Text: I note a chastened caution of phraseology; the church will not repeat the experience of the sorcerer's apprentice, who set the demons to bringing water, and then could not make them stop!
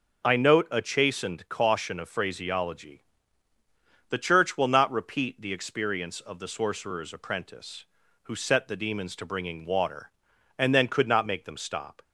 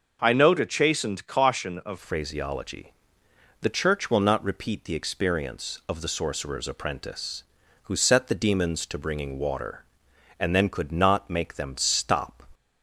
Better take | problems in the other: first | changes voice at "phraseology"; from 1.9 s on; 10.5 s long

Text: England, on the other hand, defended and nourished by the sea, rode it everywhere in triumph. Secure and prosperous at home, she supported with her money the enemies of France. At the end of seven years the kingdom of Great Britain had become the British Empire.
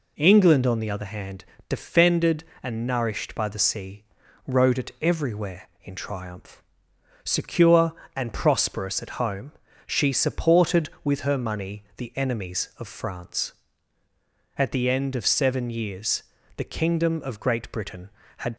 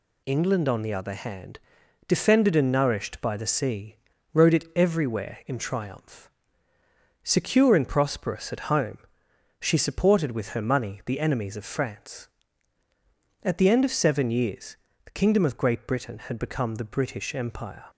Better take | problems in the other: second | pauses between "years" and "the"; slight; at 16.2 s; 0.34 s long; slight in the second // stops before "become the British Empire"; at 18.5 s

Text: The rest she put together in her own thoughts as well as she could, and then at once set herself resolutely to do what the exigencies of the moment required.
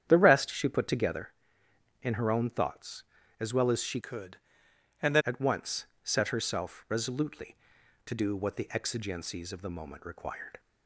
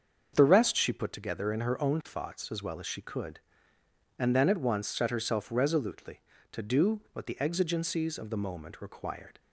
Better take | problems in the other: second | starts louder than the rest; strong; until 1.0 s; 9 dB; also in the second // changes voice from "could" to "then"; from 4.0 to 5.2 s; 1.2 s long // pauses between "once" and "set"; slight; at 5.8 s; 0.18 s long

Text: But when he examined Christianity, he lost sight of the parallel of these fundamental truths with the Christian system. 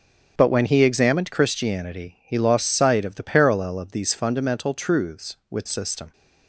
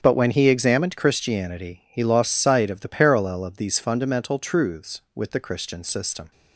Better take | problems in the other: second | starts louder than the rest; until 1.3 s; 6.5 dB; also in the second // skips "the Christian"; at 5.6 s

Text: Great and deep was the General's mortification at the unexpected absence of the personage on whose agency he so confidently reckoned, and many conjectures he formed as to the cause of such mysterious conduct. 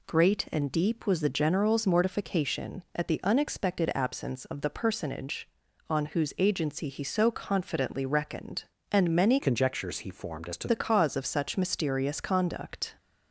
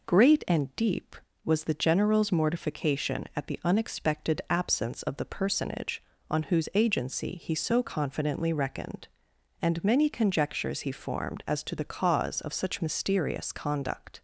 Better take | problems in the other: second | changes voice from "conjectures" to "to"; from 9.3 to 10.6 s; 1.3 s long

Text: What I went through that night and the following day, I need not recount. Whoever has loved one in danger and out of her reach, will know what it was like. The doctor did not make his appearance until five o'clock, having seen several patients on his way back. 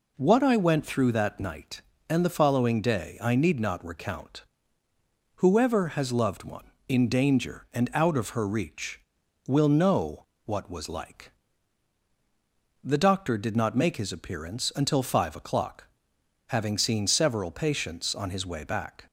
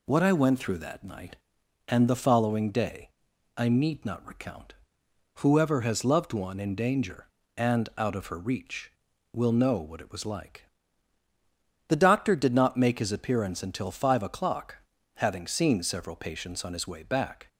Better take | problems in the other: second | pauses between "know" and "what"; slight; at 10.2 s; 0.18 s long // skips "it"; at 10.7 s

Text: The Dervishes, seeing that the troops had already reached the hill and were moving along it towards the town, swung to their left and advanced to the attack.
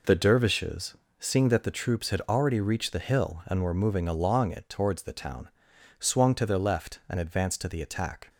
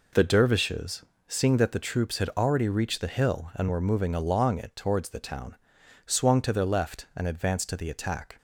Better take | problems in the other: neither | none

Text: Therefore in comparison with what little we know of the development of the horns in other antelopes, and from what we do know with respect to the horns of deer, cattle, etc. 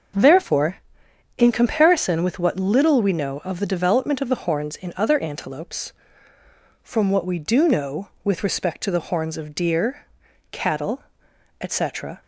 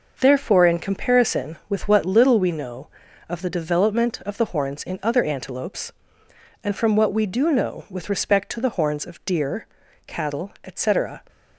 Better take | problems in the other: second | skips "and"; at 6.3 s

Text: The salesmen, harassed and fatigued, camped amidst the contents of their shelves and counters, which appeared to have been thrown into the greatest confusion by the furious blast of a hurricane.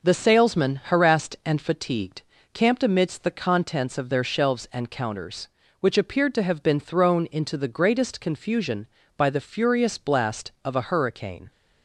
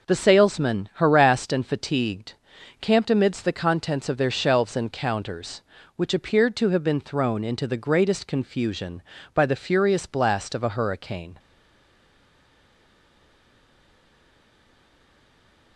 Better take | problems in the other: first | stays silent after the last word; strong; from 11.3 s on; 4.4 s long

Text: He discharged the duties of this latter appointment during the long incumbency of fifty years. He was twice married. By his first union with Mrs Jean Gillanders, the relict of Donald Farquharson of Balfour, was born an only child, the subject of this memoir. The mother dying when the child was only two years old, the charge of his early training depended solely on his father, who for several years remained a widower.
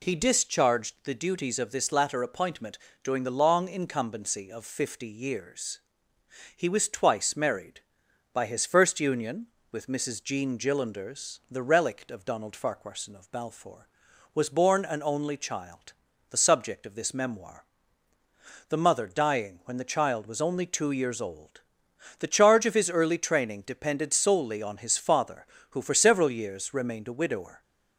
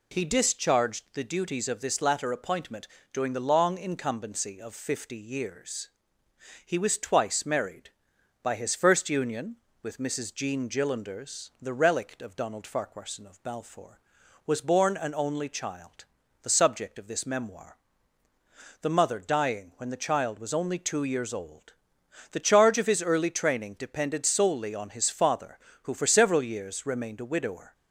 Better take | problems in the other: neither | pauses between "appointment" and "during"; slight; the same in both

